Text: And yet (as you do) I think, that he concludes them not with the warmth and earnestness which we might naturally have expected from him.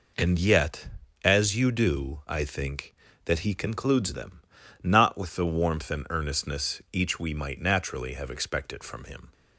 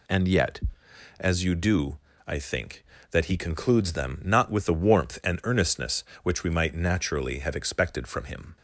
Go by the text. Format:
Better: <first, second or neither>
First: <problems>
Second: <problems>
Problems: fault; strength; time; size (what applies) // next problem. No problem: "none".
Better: second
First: pauses between "them" and "not"; at 4.4 s; 0.42 s long // says "each" for "which"; at 6.9 s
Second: none